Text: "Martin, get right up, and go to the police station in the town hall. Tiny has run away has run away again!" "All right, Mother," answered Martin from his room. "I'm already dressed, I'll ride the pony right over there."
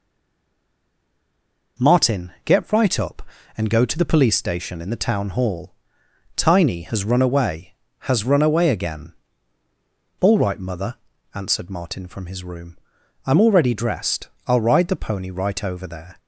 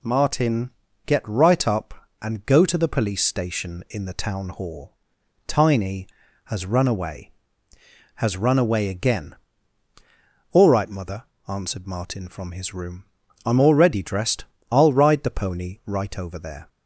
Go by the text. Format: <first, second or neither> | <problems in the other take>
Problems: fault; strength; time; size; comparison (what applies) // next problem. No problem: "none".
second | stays silent before the first word; noticeable; until 1.7 s; 1.7 s long